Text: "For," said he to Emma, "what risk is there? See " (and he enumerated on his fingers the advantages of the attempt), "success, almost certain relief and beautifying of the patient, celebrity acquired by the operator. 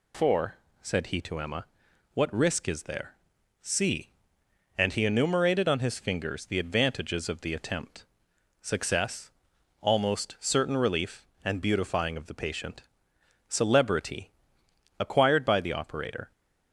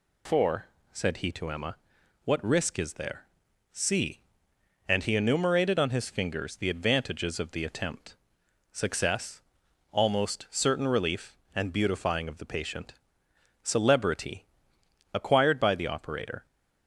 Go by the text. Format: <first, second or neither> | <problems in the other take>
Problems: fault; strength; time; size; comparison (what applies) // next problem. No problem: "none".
neither | pauses between "celebrity" and "acquired"; noticeable; the same in both